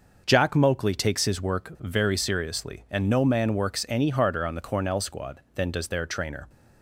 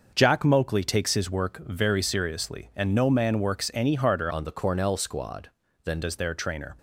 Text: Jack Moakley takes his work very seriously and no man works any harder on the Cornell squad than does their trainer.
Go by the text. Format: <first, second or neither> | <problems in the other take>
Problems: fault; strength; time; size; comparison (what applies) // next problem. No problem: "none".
first | starts louder than the rest; noticeable; until 1.1 s; 6 dB // changes voice from "on" to "than"; from 4.3 to 6.0 s; 1.7 s long